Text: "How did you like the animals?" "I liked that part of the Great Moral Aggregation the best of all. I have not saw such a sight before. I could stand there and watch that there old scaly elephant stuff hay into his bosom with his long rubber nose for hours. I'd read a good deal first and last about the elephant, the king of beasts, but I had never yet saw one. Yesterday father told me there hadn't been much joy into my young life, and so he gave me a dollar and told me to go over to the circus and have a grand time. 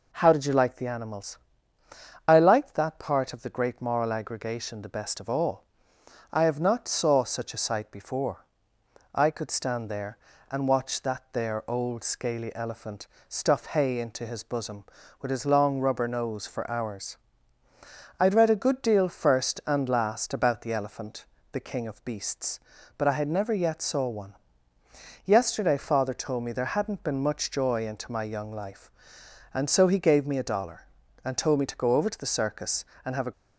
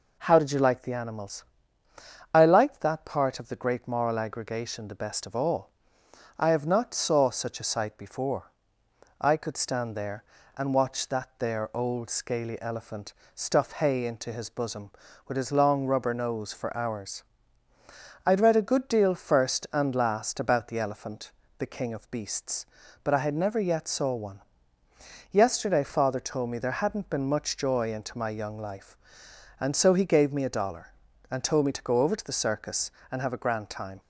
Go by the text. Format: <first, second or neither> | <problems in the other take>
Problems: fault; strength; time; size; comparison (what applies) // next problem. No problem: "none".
second | pauses between "elephant" and "stuff"; slight; at 13.0 s; 0.20 s long; slight in the second // stops before "grand time"; at 33.3 s